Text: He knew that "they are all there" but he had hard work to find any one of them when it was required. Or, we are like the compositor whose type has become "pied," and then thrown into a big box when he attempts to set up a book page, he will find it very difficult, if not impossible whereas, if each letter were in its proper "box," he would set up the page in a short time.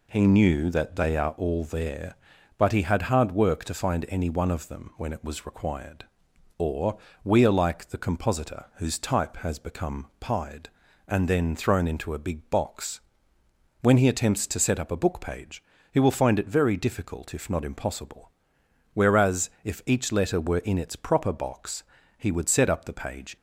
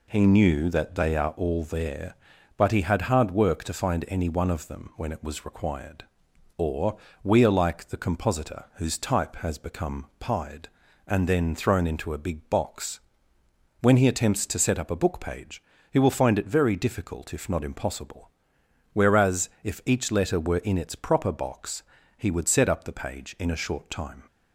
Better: second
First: pauses between "box" and "when"; noticeable; at 13.0 s; 0.82 s long // pauses between "impossible" and "whereas"; noticeable; at 18.3 s; 0.62 s long // stops before "in a short time"; at 23.3 s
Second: pauses between "box" and "when"; noticeable; at 13.0 s; 0.82 s long // pauses between "impossible" and "whereas"; noticeable; at 18.3 s; 0.62 s long

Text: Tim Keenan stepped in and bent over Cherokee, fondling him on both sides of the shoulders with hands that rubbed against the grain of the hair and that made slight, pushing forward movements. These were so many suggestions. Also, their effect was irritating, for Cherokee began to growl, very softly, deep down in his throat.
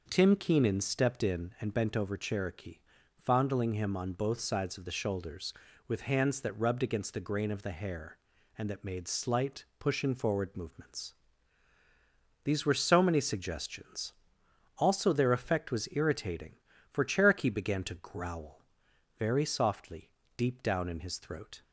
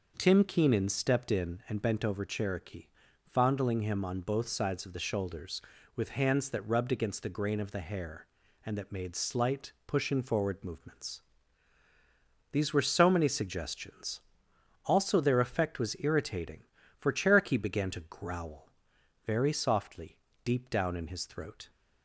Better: neither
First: none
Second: none

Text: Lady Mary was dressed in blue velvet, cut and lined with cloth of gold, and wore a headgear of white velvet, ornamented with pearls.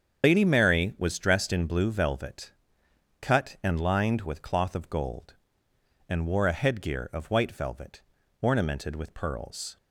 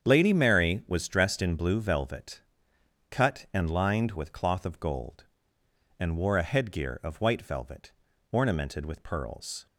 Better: second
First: loses the start of "Lady"; at 0.2 s; 95 ms // starts louder than the rest; strong; until 1.2 s; 7.5 dB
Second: starts louder than the rest; strong; until 1.0 s; 7.5 dB

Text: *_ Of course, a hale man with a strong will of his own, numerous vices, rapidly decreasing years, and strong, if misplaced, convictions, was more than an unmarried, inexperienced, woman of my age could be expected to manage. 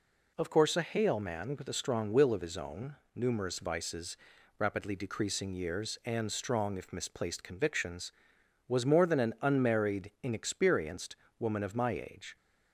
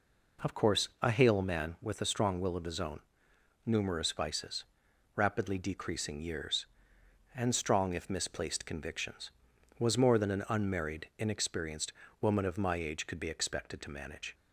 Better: second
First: stops before "could be expected to manage"; at 12.3 s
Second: none

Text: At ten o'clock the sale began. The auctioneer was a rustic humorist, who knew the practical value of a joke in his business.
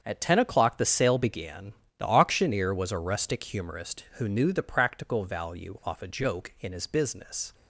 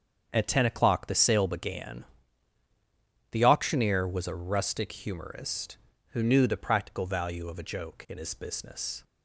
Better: second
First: starts louder than the rest; strong; until 1.0 s; 7 dB // says "off" for "of"; at 5.8 s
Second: starts louder than the rest; strong; until 1.3 s; 7 dB

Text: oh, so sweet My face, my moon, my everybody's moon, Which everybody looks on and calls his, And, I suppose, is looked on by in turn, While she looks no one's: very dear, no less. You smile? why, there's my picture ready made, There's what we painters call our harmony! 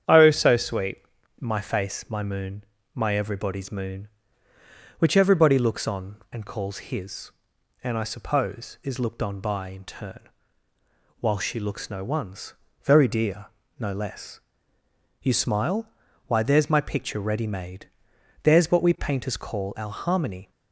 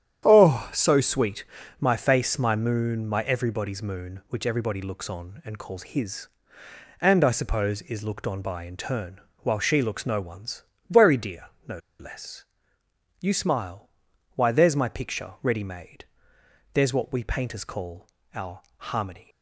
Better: first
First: starts louder than the rest; strong; until 1.4 s; 8.5 dB // pauses between "sweet" and "My"; at 0.9 s; 0.40 s long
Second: starts louder than the rest; strong; until 1.2 s; 10 dB // pauses between "sweet" and "My"; slight; at 1.4 s; 0.36 s long // pauses between "no" and "less"; slight; at 11.7 s; 0.21 s long // pauses between "call" and "our"; slight; at 18.0 s; 0.28 s long // pauses between "our" and "harmony"; slight; at 18.6 s; 0.16 s long

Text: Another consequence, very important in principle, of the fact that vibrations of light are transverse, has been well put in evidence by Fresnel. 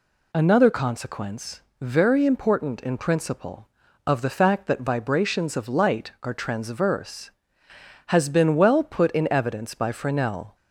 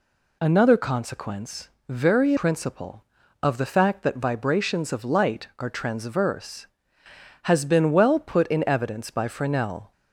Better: first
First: none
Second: skips "important in"; at 2.3 s

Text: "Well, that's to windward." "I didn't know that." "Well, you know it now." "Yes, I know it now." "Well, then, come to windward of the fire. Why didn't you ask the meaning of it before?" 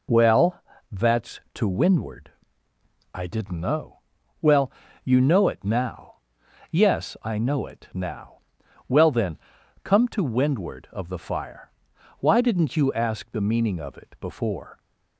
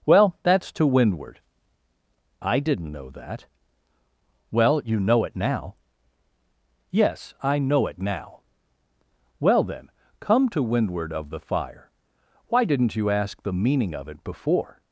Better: second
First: skips "that"; at 4.2 s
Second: none

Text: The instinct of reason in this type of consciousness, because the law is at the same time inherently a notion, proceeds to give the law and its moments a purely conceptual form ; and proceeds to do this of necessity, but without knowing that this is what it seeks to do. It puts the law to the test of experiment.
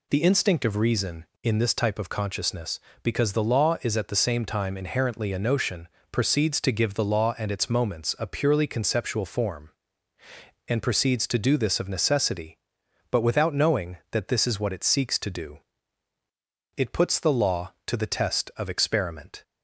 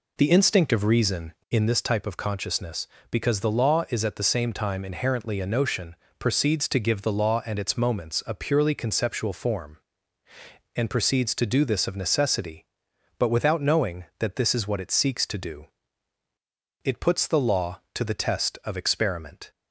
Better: first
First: none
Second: starts louder than the rest; slight; until 1.7 s; 3 dB

